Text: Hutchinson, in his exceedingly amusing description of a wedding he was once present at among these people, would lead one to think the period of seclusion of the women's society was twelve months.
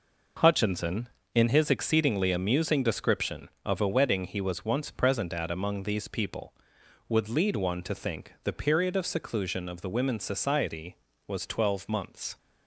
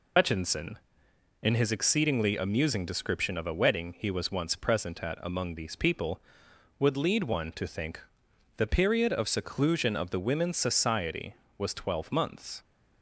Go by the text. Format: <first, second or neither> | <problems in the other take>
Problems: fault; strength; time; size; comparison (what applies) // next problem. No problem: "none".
first | loses the start of "Hutchinson"; at 0.1 s; 80 ms // pauses between "think" and "the"; noticeable; at 8.0 s; 0.56 s long